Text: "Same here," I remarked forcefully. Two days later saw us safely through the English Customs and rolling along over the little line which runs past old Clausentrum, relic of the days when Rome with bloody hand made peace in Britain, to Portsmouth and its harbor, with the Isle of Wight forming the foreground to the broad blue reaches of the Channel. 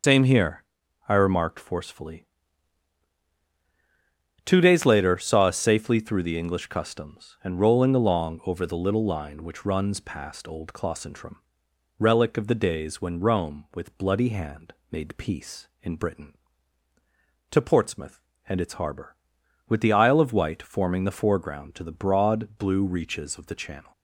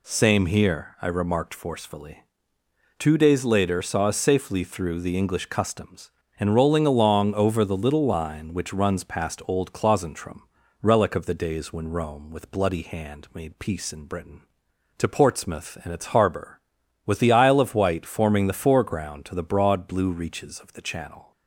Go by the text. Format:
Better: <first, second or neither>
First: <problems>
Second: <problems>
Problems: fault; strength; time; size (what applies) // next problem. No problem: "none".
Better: second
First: loses the start of "Same"; at 0.0 s; 105 ms // starts louder than the rest; until 1.4 s; 6.5 dB // pauses between "hand" and "made"; slight; at 14.7 s; 0.16 s long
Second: none